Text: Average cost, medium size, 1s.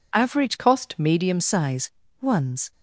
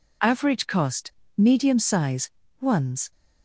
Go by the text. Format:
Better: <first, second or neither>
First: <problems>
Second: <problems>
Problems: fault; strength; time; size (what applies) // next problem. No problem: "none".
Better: second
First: changes voice from "cost" to "medium"; from 0.5 to 1.3 s; 0.8 s long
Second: none